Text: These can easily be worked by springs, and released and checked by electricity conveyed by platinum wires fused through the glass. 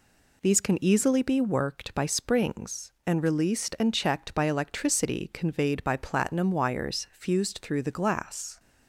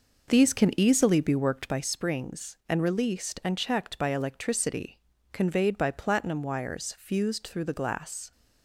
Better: first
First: none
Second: starts louder than the rest; noticeable; until 1.8 s; 5.5 dB // pauses between "electricity" and "conveyed"; slight; at 4.9 s; 0.34 s long

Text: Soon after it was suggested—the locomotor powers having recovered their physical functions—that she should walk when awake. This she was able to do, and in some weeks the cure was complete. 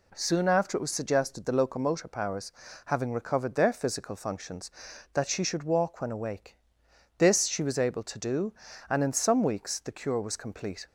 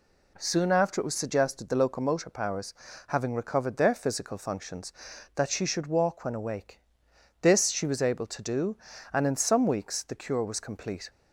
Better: neither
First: pauses between "powers" and "having"; slight; at 2.5 s; 0.34 s long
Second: pauses between "powers" and "having"; slight; at 2.7 s; 0.34 s long

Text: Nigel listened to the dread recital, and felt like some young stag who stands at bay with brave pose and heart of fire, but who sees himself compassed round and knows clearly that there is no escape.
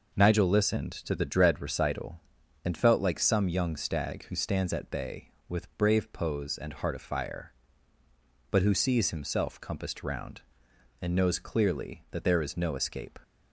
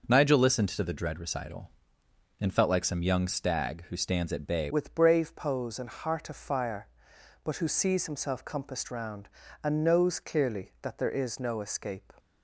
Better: first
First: none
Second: changes voice at "with"; from 4.7 s on; 7.4 s long

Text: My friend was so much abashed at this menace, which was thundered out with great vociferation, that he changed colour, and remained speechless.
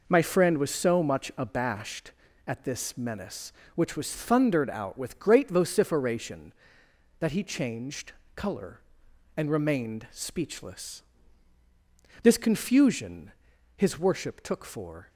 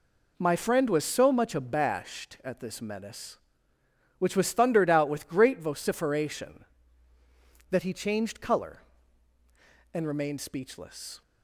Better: second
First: pauses between "changed" and "colour"; slight; at 8.1 s; 0.24 s long // goes on to say "This confusion his worship took for"; strong; from 12.2 s on; 2.8 s long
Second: none

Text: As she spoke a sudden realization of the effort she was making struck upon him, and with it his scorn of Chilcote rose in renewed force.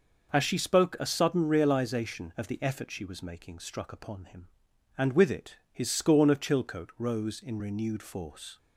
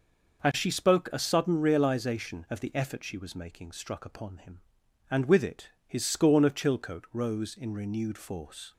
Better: neither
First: pauses between "it" and "his"; slight; at 5.5 s; 0.16 s long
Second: pauses between "it" and "his"; slight; at 5.6 s; 0.18 s long

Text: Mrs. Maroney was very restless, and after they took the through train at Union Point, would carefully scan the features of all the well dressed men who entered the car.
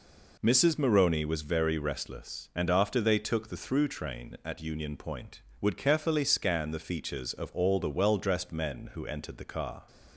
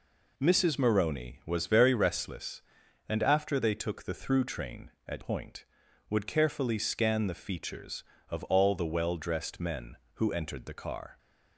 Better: first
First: none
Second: skips "Union"; at 5.2 s

